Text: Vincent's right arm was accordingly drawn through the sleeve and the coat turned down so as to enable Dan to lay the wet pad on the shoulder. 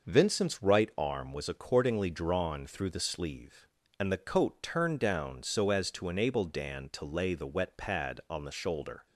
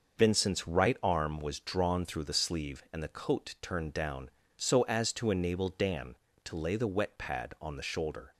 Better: first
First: none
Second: starts louder than the rest; until 1.2 s; 6 dB // skips "accordingly"; at 1.5 s

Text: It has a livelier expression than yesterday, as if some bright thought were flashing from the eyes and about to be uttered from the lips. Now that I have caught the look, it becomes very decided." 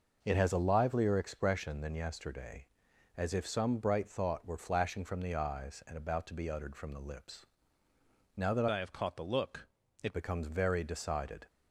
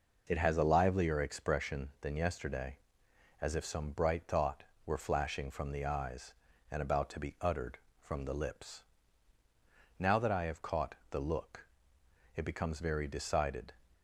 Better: second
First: changes voice from "I" to "it"; from 8.7 to 10.1 s; 1.4 s long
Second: none

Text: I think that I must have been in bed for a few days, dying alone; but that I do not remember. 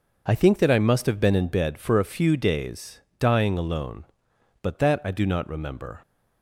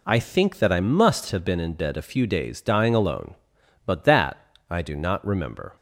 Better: first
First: none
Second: skips "for"; at 1.9 s // pauses between "that" and "I"; slight; at 4.3 s; 0.34 s long

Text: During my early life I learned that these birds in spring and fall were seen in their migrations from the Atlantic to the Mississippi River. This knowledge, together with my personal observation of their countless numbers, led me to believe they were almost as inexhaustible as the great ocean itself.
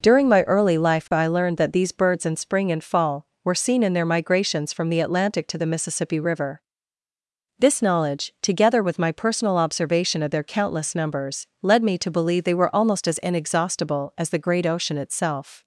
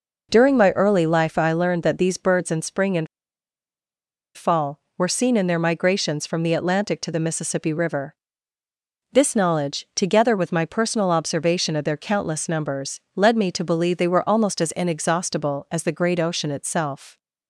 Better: first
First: none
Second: pauses between "and" and "fall"; strong; at 3.0 s; 1.3 s long

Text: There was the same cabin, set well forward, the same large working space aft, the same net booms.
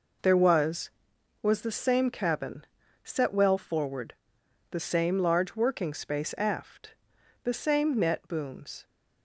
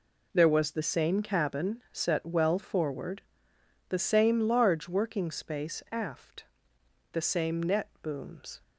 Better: second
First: says "was" twice; at 1.4 s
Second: none

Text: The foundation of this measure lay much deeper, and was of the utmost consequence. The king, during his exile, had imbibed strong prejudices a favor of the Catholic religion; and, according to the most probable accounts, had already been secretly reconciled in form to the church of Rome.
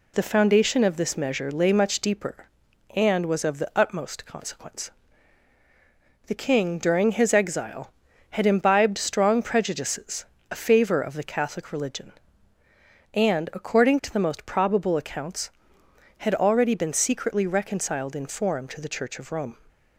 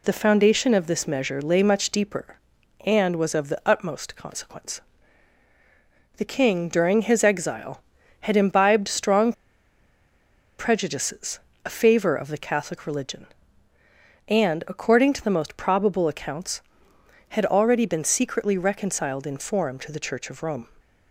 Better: first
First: pauses between "prejudices" and "a"; slight; at 10.2 s; 0.28 s long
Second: pauses between "strong" and "prejudices"; strong; at 9.3 s; 1.2 s long // pauses between "prejudices" and "a"; slight; at 11.3 s; 0.28 s long

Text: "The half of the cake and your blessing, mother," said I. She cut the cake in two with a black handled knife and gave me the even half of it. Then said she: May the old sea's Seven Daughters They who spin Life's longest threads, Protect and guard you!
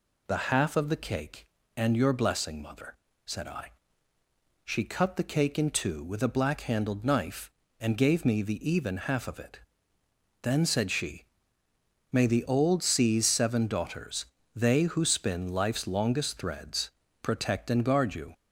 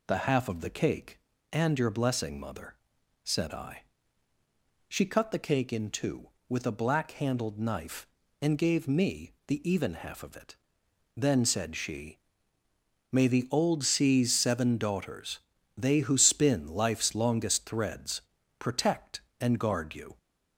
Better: neither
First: pauses between "Daughters" and "They"; slight; at 14.2 s; 0.28 s long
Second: pauses between "Daughters" and "They"; slight; at 15.3 s; 0.36 s long

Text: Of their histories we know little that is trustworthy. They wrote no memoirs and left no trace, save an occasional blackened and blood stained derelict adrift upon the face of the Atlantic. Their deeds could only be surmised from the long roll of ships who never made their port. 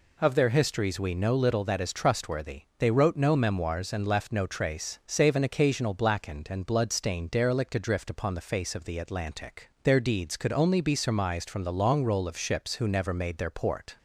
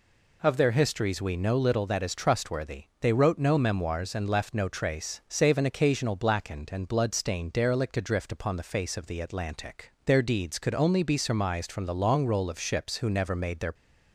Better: first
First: none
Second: stops before "port"; at 13.7 s

